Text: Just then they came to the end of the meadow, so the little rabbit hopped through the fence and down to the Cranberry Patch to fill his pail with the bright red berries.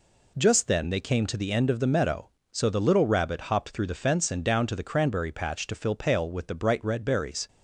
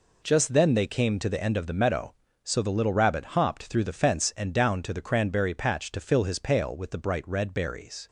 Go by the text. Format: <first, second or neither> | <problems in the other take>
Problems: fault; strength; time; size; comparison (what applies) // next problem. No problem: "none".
second | skips "his"; at 5.9 s